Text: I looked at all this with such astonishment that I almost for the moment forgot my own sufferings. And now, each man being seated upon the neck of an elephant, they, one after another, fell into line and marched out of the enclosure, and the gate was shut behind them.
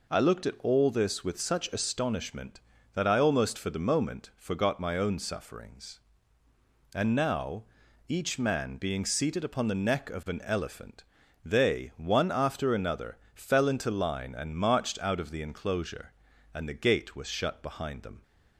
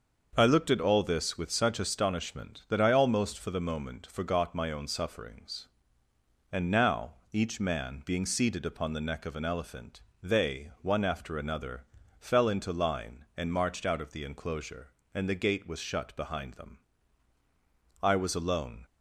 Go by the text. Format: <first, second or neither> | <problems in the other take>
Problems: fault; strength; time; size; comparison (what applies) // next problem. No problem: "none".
first | starts louder than the rest; until 1.3 s; 6.5 dB // goes on to say "I was alone"; noticeable; from 18.0 s on; 0.84 s long